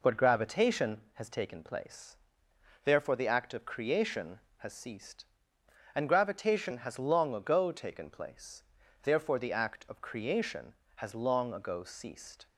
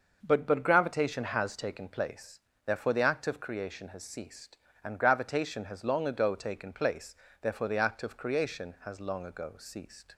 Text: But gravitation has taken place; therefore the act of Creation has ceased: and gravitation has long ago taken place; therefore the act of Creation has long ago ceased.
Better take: first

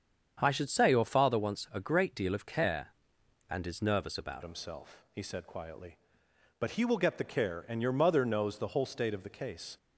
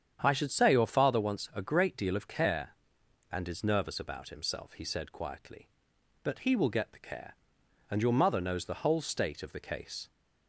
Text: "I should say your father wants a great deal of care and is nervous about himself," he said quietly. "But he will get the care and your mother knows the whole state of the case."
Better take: second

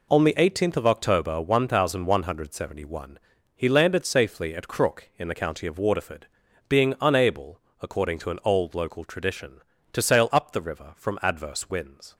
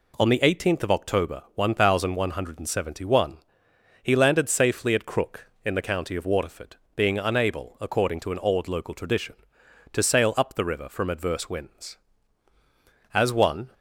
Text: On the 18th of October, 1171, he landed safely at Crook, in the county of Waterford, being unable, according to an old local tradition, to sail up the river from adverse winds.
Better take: first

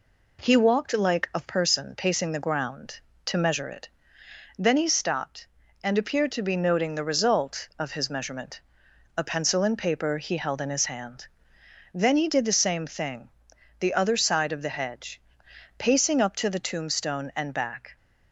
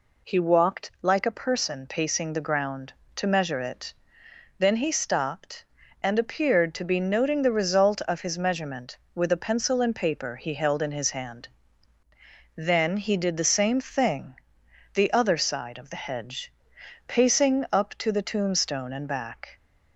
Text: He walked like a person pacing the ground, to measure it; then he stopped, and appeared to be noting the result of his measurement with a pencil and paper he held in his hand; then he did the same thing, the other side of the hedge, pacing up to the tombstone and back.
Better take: second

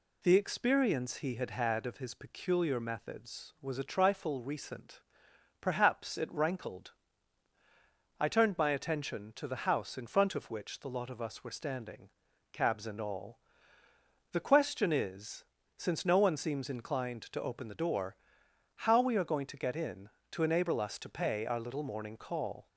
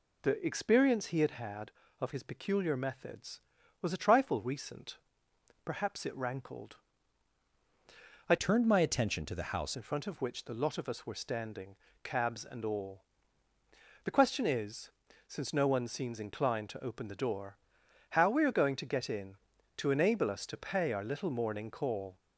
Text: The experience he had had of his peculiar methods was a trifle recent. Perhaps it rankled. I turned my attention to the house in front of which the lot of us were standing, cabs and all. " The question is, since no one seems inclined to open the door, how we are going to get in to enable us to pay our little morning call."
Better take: first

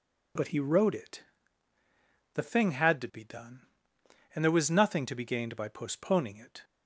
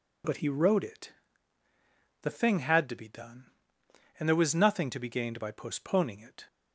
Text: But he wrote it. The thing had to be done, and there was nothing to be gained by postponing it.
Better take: neither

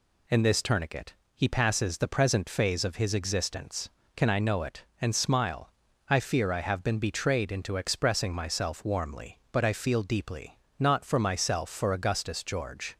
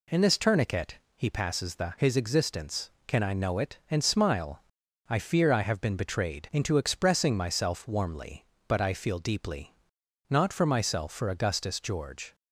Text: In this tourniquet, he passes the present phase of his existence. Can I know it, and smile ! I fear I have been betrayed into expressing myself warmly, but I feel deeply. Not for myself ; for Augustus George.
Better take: first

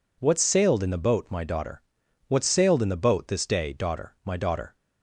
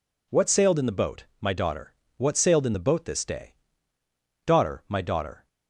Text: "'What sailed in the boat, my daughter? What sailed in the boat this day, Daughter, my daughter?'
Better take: neither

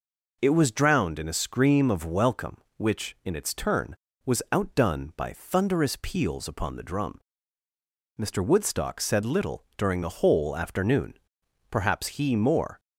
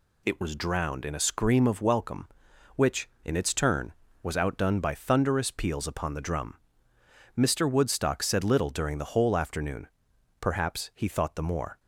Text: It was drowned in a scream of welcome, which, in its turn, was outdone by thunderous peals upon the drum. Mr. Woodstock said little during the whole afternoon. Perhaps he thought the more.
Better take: second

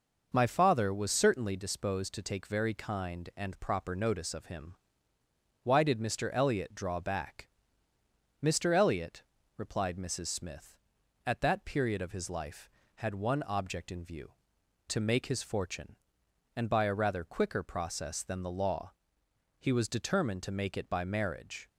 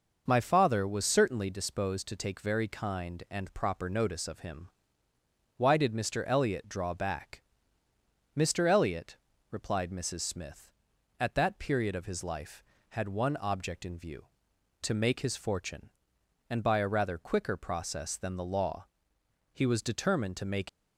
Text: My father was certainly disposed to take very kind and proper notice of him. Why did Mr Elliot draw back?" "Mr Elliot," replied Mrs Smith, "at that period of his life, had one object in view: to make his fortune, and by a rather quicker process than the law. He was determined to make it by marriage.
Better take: first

